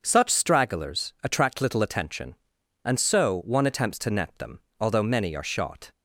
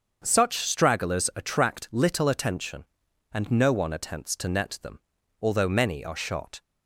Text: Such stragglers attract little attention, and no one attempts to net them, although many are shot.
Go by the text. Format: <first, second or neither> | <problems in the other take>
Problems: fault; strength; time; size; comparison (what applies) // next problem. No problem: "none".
second | starts louder than the rest; until 1.0 s; 6.5 dB; also in the second // says "so" for "no"; at 2.9 s